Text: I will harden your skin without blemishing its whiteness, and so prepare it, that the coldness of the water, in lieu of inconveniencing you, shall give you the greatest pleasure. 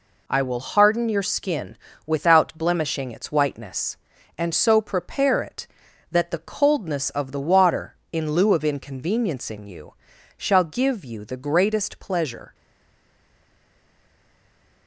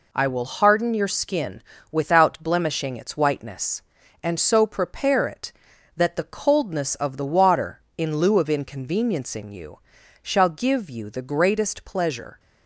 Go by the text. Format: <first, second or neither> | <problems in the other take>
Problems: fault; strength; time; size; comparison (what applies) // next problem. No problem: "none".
second | pauses between "skin" and "without"; slight; at 1.7 s; 0.30 s long; slight in the second // stays silent after the last word; from 12.5 s on; 2.3 s long